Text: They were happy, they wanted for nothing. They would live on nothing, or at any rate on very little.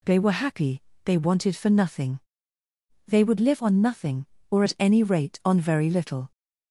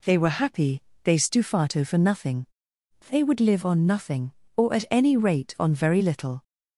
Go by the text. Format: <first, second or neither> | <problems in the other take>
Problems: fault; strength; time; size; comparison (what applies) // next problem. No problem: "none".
first | says "stufato" for "wanted"; at 1.1 s